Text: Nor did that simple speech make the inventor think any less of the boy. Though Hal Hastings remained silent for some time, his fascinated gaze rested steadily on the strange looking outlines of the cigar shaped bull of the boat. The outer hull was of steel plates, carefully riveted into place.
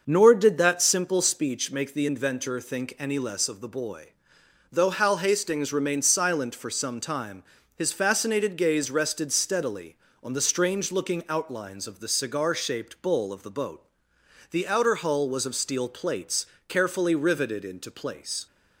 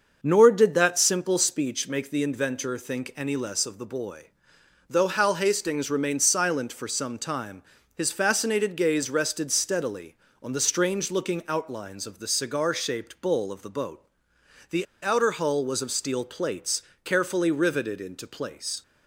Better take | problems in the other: first | starts louder than the rest; until 1.2 s; 6 dB; also in the first // pauses between "The" and "outer"; slight; at 14.8 s; 0.16 s long

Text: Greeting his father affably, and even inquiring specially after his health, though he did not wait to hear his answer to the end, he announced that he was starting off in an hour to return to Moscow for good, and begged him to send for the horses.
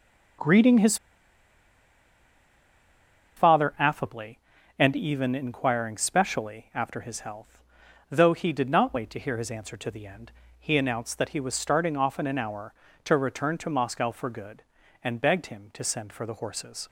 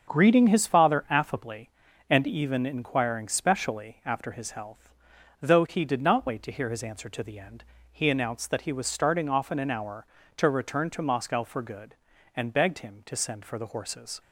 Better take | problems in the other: second | starts louder than the rest; strong; until 3.8 s; 7 dB; also in the second // pauses between "his" and "father"; strong; at 0.9 s; 2.4 s long

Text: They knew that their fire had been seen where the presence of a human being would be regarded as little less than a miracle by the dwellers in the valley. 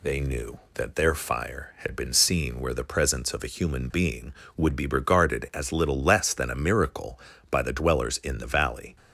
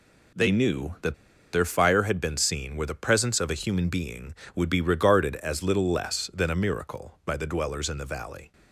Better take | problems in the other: first | pauses between "that" and "their"; at 1.1 s; 0.39 s long

